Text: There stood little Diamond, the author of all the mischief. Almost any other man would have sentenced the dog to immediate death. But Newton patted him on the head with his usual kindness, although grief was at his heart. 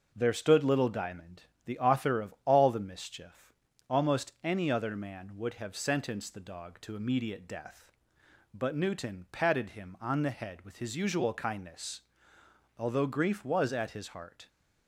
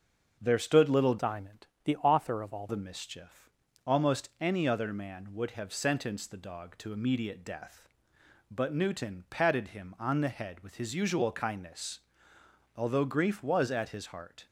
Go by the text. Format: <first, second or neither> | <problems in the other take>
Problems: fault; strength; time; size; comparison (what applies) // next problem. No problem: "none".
first | starts louder than the rest; until 1.4 s; 6.5 dB // changes voice from "Diamond" to "all"; from 1.1 to 2.6 s; 1.5 s long